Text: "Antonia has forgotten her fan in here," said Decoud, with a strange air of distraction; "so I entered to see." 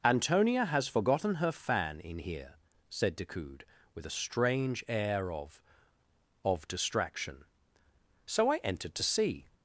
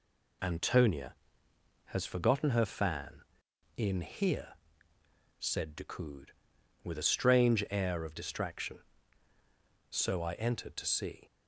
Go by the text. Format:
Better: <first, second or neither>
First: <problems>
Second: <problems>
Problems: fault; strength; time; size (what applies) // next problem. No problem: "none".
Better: second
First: says "of" twice; at 6.4 s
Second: none